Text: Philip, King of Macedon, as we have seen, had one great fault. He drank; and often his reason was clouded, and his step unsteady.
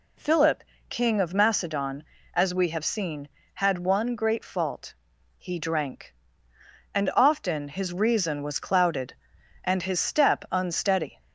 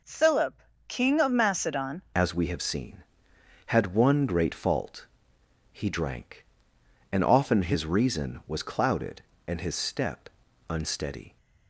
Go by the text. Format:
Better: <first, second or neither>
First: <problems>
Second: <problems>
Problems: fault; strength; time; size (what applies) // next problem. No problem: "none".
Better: first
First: none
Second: changes voice at "as"; from 2.1 s on; 9.2 s long // pauses between "step" and "unsteady"; at 10.2 s; 0.40 s long